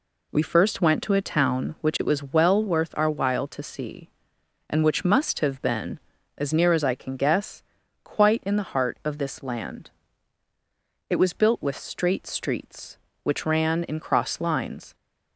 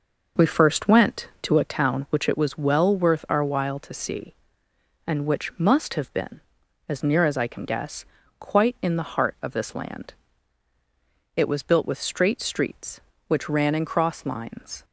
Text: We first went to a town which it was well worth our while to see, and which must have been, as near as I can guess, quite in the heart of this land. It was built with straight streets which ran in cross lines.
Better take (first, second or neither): first